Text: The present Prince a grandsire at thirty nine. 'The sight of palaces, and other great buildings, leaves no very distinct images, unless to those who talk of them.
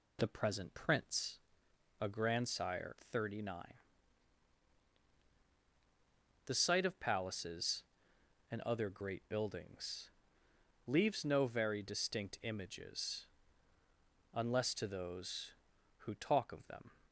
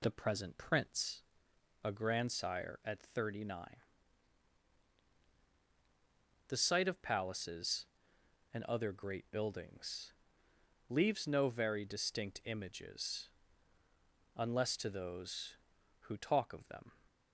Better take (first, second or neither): second